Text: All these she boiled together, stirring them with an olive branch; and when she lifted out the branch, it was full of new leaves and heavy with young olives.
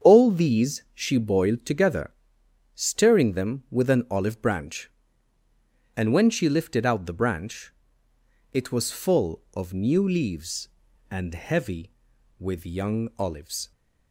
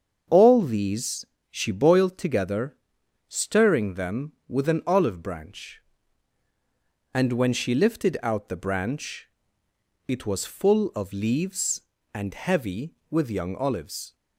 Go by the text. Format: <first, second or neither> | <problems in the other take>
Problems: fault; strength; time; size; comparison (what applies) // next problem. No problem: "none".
first | starts louder than the rest; strong; until 1.5 s; 7 dB; strong in the first // pauses between "these" and "she"; slight; at 1.2 s; 0.26 s long // skips "new"; at 11.1 s